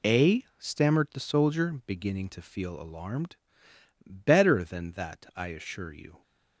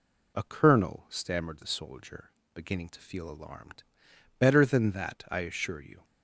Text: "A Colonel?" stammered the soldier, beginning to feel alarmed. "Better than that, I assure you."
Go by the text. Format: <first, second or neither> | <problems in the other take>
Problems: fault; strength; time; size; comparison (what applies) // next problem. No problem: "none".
second | skips "Colonel"; at 0.4 s